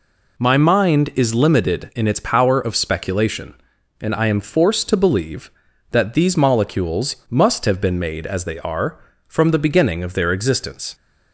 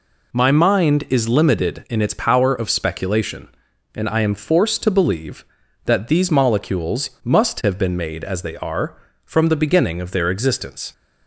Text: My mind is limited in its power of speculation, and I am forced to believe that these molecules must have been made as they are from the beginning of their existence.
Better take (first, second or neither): neither